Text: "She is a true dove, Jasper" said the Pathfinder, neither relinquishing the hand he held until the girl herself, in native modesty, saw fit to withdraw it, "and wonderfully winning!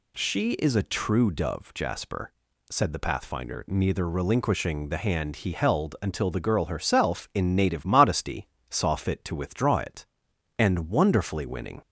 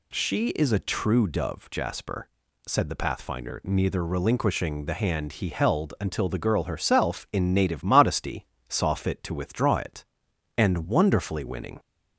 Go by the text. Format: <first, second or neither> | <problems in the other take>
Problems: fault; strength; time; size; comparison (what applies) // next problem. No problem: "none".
neither | pauses between "Jasper" and "said"; the same in both